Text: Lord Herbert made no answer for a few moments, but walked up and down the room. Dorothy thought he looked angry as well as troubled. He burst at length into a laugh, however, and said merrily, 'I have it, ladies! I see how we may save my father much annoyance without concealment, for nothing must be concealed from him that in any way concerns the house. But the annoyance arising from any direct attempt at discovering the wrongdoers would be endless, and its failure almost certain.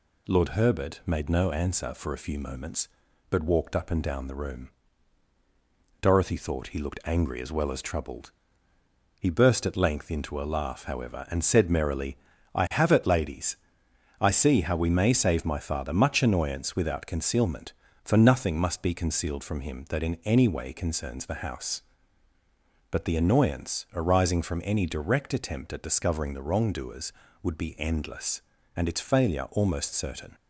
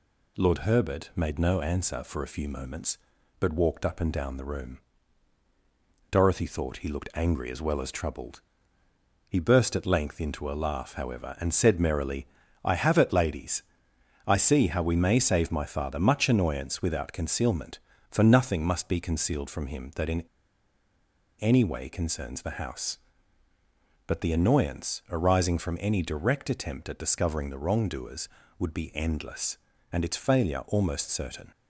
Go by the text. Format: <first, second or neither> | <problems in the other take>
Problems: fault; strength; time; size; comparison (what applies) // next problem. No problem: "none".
first | pauses between "in" and "any"; at 20.2 s; 1.1 s long